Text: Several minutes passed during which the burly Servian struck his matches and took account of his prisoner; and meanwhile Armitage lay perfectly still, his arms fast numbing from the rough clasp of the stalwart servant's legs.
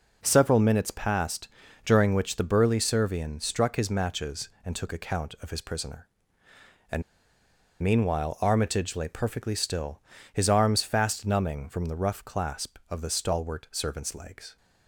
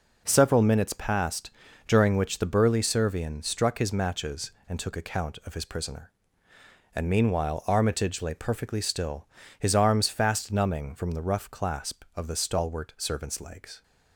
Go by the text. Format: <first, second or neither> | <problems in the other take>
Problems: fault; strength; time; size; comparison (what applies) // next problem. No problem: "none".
second | pauses between "passed" and "during"; slight; at 1.4 s; 0.36 s long; slight in the second // pauses between "and" and "meanwhile"; noticeable; at 7.0 s; 0.78 s long